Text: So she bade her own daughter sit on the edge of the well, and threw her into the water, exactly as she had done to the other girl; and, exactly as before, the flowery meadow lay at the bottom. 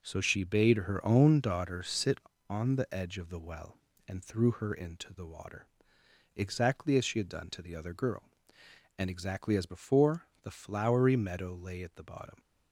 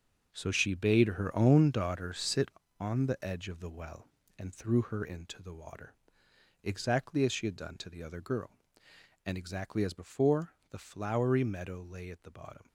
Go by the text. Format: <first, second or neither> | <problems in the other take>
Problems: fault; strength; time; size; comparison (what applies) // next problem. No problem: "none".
first | gets quieter; strong; throughout; 9.5 dB